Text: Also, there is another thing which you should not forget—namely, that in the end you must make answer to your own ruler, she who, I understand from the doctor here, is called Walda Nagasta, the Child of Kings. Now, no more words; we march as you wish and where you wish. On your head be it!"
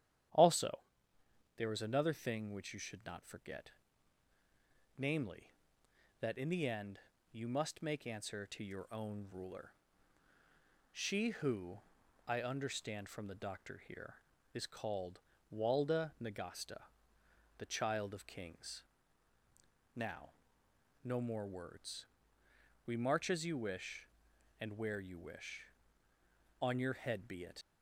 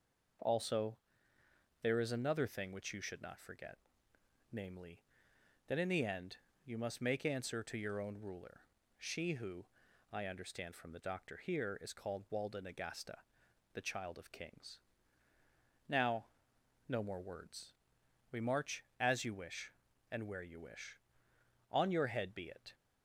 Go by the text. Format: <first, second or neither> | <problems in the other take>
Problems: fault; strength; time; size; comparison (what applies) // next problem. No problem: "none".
second | starts louder than the rest; strong; until 2.1 s; 10.5 dB // pauses between "end" and "you"; slight; at 6.9 s; 0.32 s long; slight in the second // pauses between "called" and "Walda"; slight; at 15.1 s; 0.34 s long // leaves "it" unfinished; at 27.6 s; 85 ms